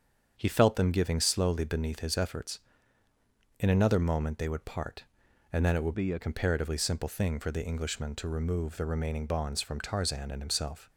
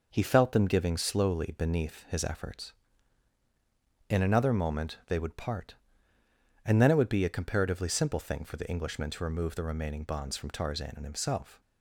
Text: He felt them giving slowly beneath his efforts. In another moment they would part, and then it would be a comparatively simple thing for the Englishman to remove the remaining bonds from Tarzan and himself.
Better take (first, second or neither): second